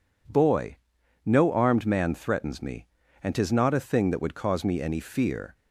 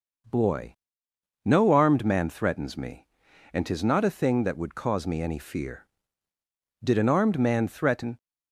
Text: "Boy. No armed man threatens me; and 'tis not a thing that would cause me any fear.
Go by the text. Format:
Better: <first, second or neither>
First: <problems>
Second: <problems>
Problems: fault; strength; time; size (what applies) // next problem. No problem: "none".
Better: first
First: none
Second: goes on to say "Did an armed man threaten"; from 6.8 s on; 1.3 s long